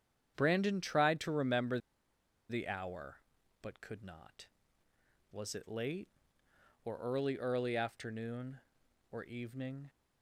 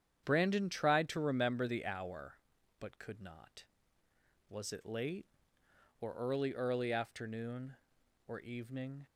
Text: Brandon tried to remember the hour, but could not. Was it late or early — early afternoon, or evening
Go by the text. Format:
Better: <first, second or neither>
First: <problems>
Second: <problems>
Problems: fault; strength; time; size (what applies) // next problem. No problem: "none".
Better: second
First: starts louder than the rest; strong; until 1.3 s; 8.5 dB // pauses between "remember" and "the"; noticeable; at 1.7 s; 0.70 s long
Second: starts louder than the rest; strong; until 1.2 s; 8.5 dB